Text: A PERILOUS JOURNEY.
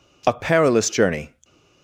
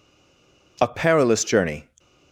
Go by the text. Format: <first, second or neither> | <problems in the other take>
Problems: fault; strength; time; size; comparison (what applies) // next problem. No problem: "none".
first | stays silent before the first word; slight; until 0.7 s; 0.7 s long